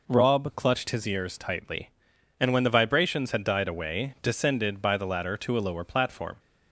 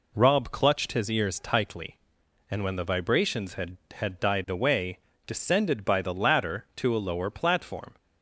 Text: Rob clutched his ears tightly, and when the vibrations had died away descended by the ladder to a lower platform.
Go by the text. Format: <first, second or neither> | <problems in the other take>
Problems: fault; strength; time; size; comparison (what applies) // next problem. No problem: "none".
first | says "had" twice; at 3.9 s // pauses between "away" and "descended"; slight; at 4.9 s; 0.26 s long